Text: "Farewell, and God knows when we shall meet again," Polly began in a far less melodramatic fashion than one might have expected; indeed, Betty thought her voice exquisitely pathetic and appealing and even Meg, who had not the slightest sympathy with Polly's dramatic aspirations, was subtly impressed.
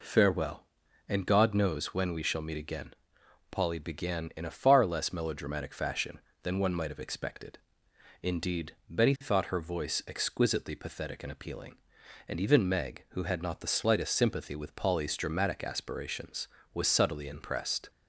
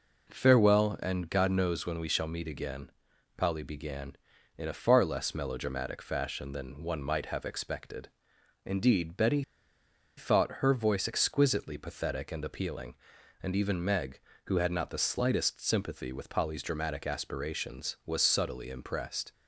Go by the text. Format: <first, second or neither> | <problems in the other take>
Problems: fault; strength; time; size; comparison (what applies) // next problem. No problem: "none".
first | pauses between "Betty" and "thought"; noticeable; at 9.4 s; 0.75 s long